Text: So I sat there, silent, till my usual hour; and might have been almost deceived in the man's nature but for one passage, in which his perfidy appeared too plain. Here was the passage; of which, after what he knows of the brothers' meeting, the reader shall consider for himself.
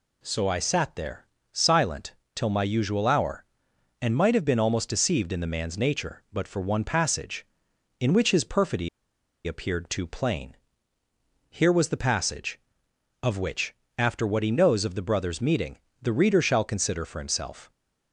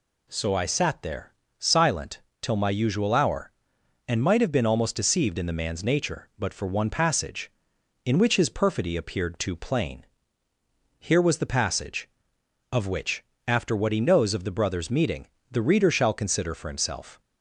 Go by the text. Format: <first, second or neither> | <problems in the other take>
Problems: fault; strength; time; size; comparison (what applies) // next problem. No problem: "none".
second | pauses between "perfidy" and "appeared"; noticeable; at 8.8 s; 0.58 s long